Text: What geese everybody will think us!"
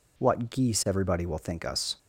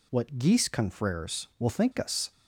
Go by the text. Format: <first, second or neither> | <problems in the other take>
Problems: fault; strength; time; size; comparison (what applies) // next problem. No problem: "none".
first | says "confreres" for "everybody"; at 0.6 s